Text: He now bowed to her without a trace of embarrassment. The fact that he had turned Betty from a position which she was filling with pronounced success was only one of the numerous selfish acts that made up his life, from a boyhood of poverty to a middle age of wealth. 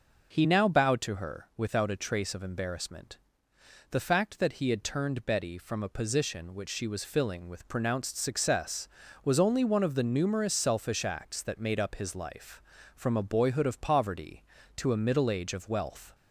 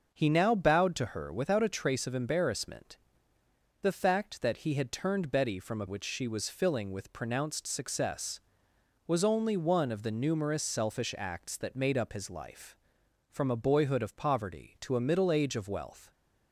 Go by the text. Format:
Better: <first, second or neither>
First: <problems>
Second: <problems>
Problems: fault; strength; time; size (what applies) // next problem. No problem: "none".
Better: first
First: none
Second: starts louder than the rest; until 1.1 s; 6 dB // skips "position"; at 5.8 s